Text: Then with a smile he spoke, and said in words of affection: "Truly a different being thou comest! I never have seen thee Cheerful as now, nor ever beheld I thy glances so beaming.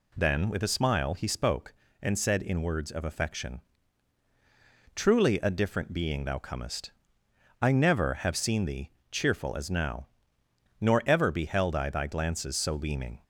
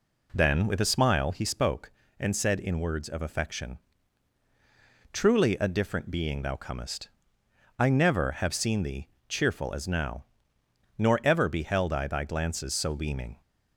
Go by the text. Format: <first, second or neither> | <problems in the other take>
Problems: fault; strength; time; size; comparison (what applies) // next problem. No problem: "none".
first | starts louder than the rest; slight; until 1.4 s; 3.5 dB // pauses between "thee" and "Cheerful"; slight; at 9.0 s; 0.18 s long; slight in the first